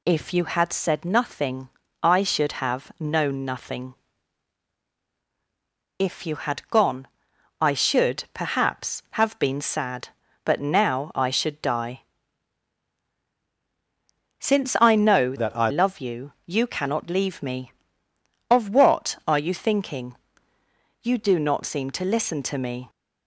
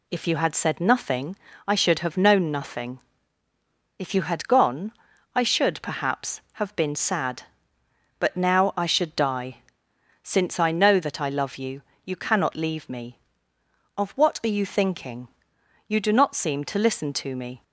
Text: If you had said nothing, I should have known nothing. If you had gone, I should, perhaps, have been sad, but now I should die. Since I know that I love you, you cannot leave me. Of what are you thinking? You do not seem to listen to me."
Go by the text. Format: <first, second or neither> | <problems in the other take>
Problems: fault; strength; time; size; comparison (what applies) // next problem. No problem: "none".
second | changes voice from "that" to "I"; from 15.3 to 15.6 s; 0.3 s long